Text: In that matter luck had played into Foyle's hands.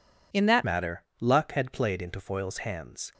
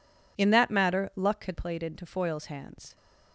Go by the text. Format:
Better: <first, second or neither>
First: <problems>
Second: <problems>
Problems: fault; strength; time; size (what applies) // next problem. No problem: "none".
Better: second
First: changes voice at "matter"; from 0.6 s on; 2.5 s long // pauses between "matter" and "luck"; slight; at 1.0 s; 0.18 s long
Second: none